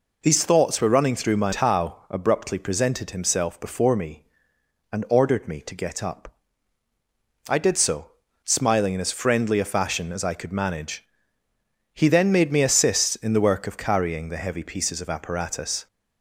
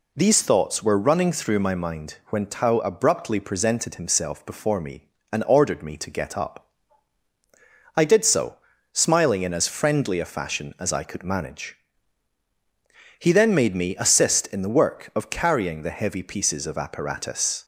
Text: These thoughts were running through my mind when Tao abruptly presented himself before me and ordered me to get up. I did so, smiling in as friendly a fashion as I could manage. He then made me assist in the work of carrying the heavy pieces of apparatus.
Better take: second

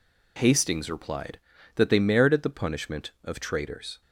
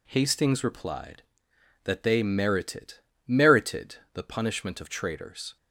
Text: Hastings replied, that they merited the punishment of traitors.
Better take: first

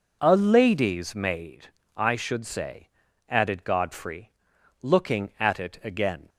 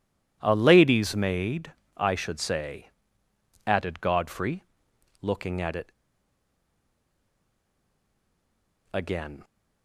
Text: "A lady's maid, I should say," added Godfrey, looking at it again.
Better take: first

